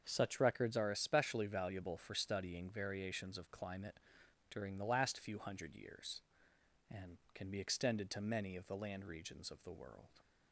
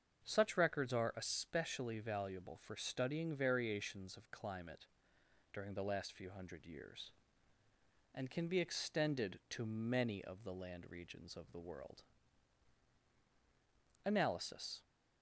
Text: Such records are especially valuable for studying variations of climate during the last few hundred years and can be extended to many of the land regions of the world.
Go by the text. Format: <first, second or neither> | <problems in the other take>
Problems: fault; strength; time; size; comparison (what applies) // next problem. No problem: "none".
first | starts louder than the rest; until 1.2 s; 7 dB; also in the first // pauses between "climate" and "during"; noticeable; at 4.8 s; 0.68 s long; noticeable in the first // goes on to say "Analysis"; noticeable; from 14.0 s on; 0.78 s long